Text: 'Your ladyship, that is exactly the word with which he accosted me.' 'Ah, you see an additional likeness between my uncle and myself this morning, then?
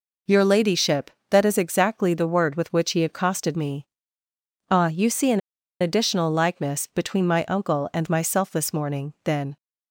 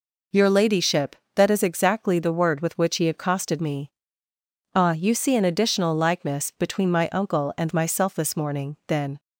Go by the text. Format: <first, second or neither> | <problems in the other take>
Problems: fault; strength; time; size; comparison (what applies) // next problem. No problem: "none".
second | pauses between "an" and "additional"; at 5.3 s; 0.40 s long